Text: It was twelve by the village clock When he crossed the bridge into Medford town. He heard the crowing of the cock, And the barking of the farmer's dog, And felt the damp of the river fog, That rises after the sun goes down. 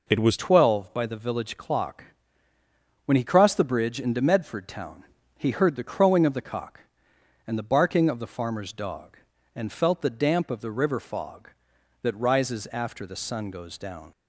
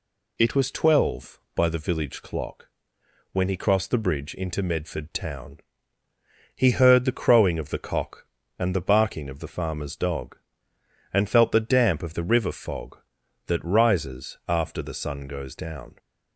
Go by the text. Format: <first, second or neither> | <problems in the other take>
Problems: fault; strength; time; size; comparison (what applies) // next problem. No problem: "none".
second | changes voice at "twelve"; from 0.3 s on; 13.8 s long // pauses between "clock" and "When"; at 2.0 s; 1.0 s long; noticeable in the second